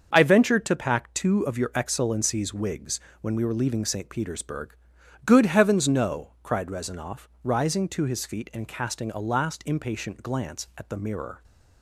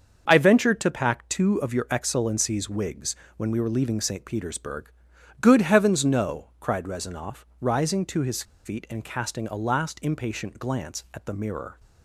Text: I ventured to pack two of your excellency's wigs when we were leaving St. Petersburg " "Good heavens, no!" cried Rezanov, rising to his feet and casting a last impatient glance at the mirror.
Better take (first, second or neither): first